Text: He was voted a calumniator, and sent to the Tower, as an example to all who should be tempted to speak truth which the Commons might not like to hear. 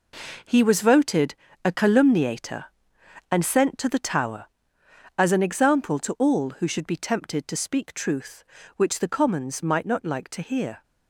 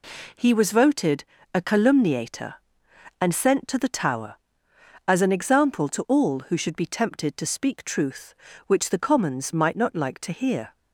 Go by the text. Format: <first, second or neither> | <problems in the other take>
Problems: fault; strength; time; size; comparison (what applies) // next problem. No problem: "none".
second | gets quieter; strong; throughout; 9.5 dB // pauses between "voted" and "a"; slight; at 1.3 s; 0.30 s long; slight in the second